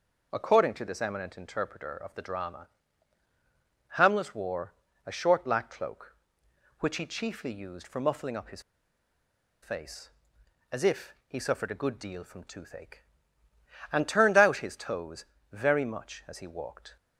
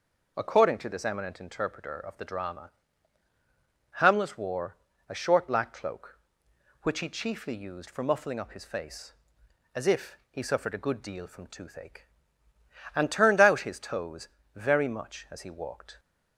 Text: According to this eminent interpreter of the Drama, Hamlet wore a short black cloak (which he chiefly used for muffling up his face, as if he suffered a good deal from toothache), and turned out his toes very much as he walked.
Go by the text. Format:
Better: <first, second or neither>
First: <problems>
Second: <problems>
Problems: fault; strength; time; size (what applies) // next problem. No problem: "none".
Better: second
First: pauses between "wore" and "a"; slight; at 4.7 s; 0.32 s long // pauses between "his" and "face"; at 8.6 s; 1.0 s long // pauses between "toes" and "very"; slight; at 15.2 s; 0.26 s long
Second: pauses between "wore" and "a"; slight; at 4.7 s; 0.32 s long // pauses between "toes" and "very"; slight; at 14.2 s; 0.26 s long